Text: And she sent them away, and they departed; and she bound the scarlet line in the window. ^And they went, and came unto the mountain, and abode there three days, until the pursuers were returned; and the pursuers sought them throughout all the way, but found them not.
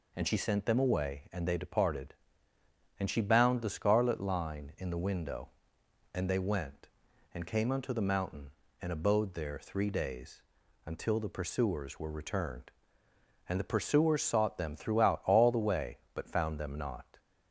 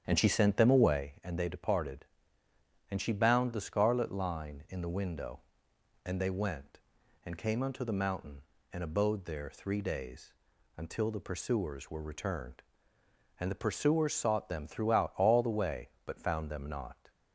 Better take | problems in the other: first | starts louder than the rest; strong; until 1.0 s; 8.5 dB

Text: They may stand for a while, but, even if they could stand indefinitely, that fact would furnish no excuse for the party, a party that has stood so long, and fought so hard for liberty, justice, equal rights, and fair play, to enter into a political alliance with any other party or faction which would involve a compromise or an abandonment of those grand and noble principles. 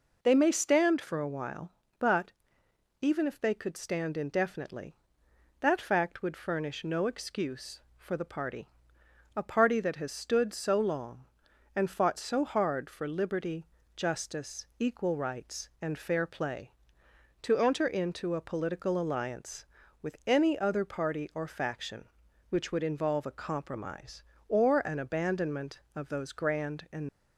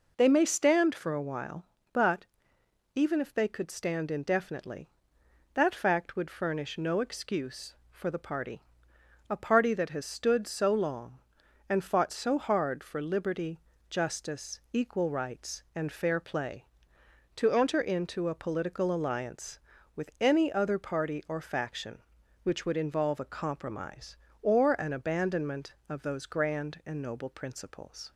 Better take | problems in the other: second | stops before "noble principles"; at 27.0 s

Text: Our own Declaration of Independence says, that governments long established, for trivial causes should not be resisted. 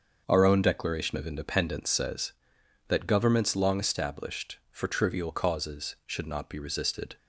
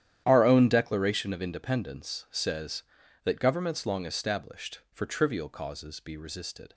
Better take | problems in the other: first | starts louder than the rest; strong; until 1.2 s; 11 dB; also in the first // skips "should not"; at 5.9 s

